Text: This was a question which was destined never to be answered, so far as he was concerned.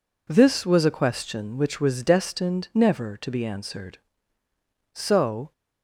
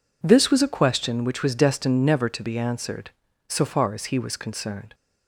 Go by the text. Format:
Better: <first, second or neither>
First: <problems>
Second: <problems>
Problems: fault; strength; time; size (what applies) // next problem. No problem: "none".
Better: second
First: stops before "far as he was concerned"; at 5.5 s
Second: none